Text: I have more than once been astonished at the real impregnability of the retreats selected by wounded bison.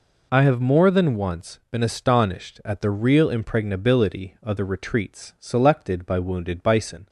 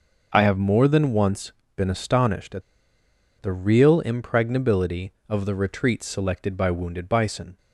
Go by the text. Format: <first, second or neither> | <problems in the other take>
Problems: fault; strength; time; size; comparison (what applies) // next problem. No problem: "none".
first | starts louder than the rest; noticeable; until 1.3 s; 6 dB // pauses between "once" and "been"; slight; at 1.5 s; 0.24 s long // pauses between "at" and "the"; noticeable; at 2.6 s; 0.78 s long